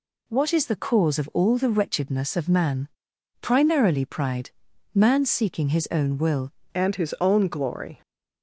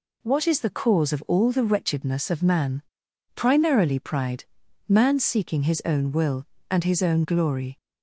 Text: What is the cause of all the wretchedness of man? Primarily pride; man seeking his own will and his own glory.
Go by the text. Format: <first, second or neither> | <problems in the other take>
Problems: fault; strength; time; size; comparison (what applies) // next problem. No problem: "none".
second | changes voice at "and"; from 6.7 s on; 1.3 s long